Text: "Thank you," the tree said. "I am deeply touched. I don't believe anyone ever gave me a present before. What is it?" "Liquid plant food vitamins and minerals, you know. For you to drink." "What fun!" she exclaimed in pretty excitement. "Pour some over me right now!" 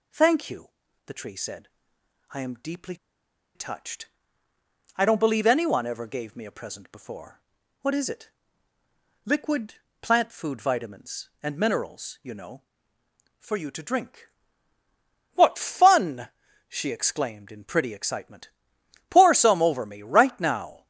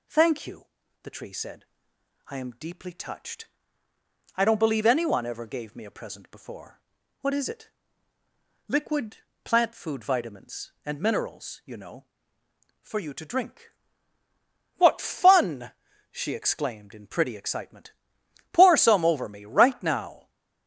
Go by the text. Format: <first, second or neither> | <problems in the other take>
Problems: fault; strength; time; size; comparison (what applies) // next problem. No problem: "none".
second | pauses between "deeply" and "touched"; noticeable; at 2.9 s; 0.60 s long // pauses between "Liquid" and "plant"; slight; at 9.7 s; 0.26 s long; slight in the second